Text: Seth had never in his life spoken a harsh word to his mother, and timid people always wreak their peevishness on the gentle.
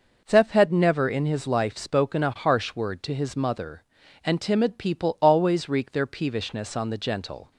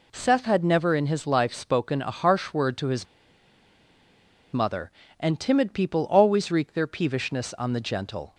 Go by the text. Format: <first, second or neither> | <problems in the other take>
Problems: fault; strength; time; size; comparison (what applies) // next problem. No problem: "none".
first | pauses between "his" and "mother"; strong; at 3.0 s; 1.4 s long